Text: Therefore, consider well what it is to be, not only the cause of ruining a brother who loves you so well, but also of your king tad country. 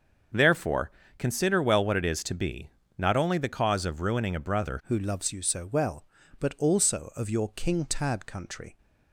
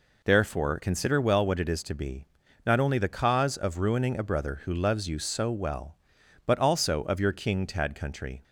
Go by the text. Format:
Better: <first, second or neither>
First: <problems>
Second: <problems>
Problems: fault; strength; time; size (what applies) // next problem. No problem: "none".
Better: second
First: starts louder than the rest; until 1.6 s; 7 dB // changes voice at "who"; from 4.8 s on; 3.9 s long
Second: none